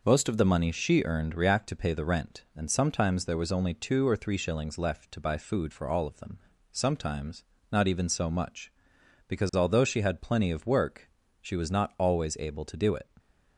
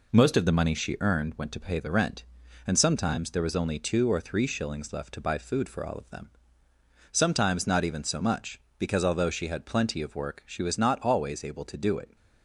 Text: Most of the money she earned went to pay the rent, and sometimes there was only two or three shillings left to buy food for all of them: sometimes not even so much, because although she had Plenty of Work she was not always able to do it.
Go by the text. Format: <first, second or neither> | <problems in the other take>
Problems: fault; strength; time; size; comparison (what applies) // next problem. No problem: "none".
second | says "react" for "went"; at 1.3 s // pauses between "sometimes" and "not"; slight; at 7.4 s; 0.28 s long // pauses between "Work" and "she"; slight; at 11.0 s; 0.32 s long